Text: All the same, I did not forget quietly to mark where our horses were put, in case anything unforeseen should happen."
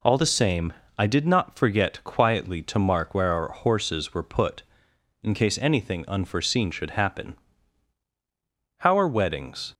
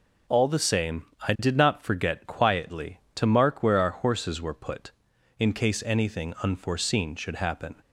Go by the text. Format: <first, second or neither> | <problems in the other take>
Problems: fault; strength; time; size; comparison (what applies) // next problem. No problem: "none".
second | goes on to say "How are weddings"; noticeable; from 8.7 s on; 0.96 s long